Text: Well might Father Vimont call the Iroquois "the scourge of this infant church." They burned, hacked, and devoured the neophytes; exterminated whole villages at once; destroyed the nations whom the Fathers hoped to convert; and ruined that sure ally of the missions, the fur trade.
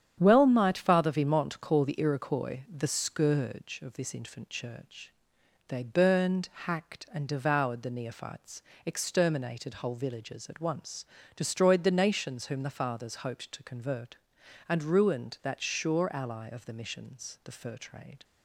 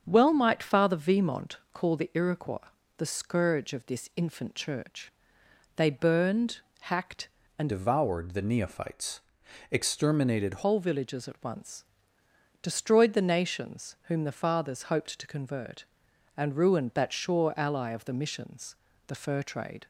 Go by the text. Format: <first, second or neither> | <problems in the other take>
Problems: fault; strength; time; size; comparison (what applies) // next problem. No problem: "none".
first | starts louder than the rest; strong; until 1.0 s; 7.5 dB; strong in the first // pauses between "Vimont" and "call"; slight; at 1.5 s; 0.16 s long // pauses between "Iroquois" and "the"; slight; at 2.6 s; 0.30 s long // changes voice from "devoured" to "exterminated"; from 7.6 to 10.6 s; 3.0 s long